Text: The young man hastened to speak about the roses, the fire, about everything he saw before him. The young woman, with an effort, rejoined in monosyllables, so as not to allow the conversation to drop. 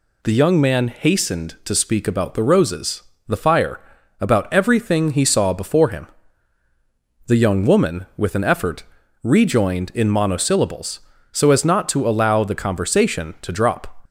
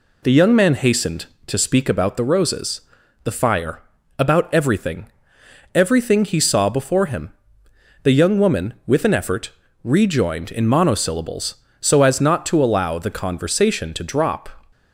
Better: first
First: none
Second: says "everything" twice; at 5.7 s

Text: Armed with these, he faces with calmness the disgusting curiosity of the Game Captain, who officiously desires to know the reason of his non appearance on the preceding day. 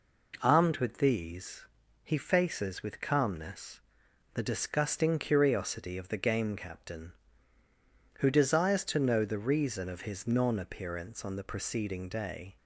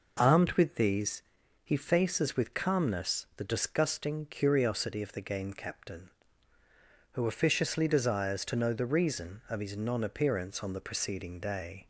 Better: second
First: pauses between "calmness" and "the"; noticeable; at 3.8 s; 0.54 s long // skips "officiously"; at 8.2 s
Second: none

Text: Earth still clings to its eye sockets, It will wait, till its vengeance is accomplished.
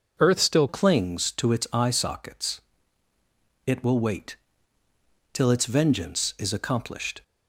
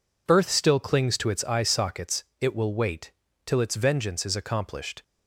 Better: second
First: changes voice at "clings"; from 0.6 s on; 6.6 s long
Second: none

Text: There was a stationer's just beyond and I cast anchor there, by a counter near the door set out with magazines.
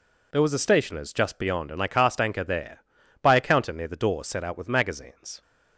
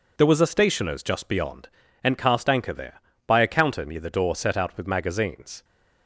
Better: first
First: none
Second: skips "I"; at 2.1 s

